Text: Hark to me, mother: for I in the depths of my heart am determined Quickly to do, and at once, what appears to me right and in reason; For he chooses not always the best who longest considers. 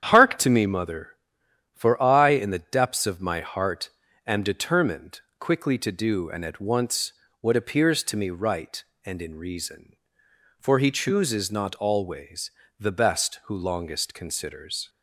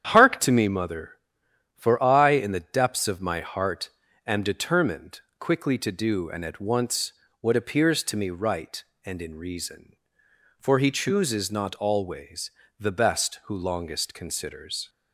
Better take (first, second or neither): neither